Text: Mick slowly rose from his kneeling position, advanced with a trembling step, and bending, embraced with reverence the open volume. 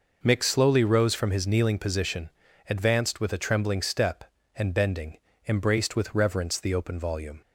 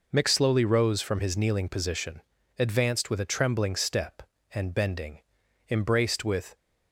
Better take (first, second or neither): first